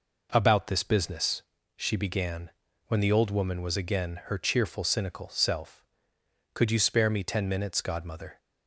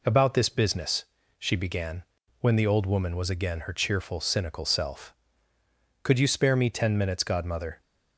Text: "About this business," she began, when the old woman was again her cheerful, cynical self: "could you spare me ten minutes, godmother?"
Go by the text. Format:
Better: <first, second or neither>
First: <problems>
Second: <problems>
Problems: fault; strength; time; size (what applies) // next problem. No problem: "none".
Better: neither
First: none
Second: none